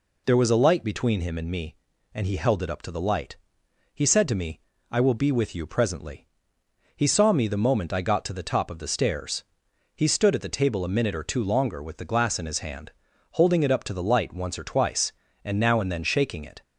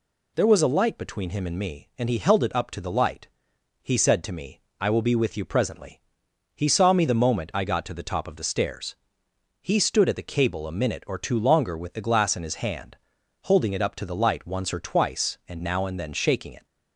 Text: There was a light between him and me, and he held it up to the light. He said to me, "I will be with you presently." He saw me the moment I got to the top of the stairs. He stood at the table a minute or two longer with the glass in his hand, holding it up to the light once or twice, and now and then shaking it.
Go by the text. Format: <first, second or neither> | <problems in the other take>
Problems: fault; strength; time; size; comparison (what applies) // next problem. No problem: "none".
first | says "cable" for "table"; at 10.3 s